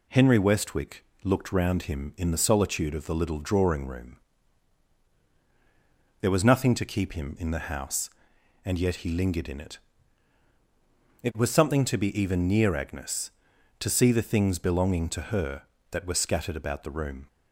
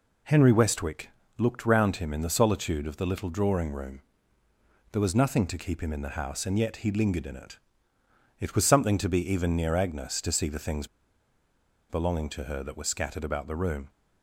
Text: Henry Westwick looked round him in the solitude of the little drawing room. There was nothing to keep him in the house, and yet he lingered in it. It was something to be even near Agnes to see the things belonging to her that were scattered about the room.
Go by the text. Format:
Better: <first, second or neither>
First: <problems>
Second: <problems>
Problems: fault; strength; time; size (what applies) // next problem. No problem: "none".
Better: first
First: pauses between "Westwick" and "looked"; slight; at 1.0 s; 0.18 s long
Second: pauses between "Westwick" and "looked"; slight; at 1.0 s; 0.28 s long // pauses between "things" and "belonging"; at 10.8 s; 1.0 s long